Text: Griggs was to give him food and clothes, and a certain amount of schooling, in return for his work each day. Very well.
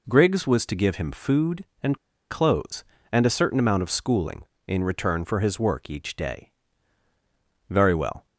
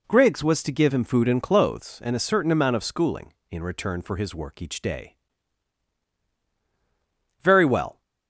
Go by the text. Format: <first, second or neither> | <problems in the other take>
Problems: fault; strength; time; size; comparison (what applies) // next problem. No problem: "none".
second | pauses between "and" and "clothes"; slight; at 1.9 s; 0.34 s long